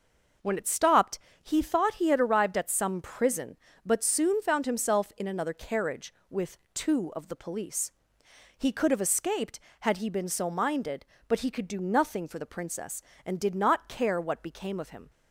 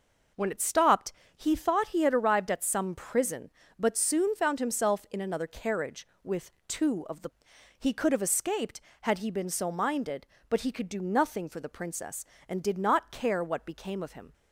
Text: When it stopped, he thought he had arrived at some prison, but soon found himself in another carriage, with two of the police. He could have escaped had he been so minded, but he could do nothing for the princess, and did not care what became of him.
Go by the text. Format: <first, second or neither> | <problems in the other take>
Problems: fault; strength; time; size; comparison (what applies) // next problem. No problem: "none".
first | pauses between "with" and "two"; slight; at 6.5 s; 0.16 s long; slight in the first // skips "police"; at 7.5 s